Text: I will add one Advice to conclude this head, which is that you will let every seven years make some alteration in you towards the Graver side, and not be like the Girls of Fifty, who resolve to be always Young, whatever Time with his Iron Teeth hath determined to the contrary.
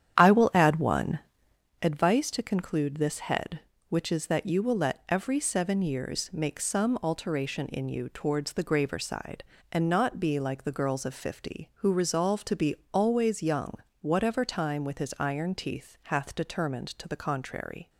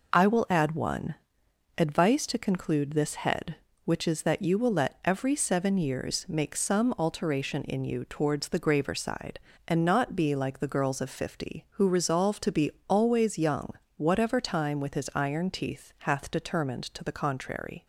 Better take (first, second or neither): second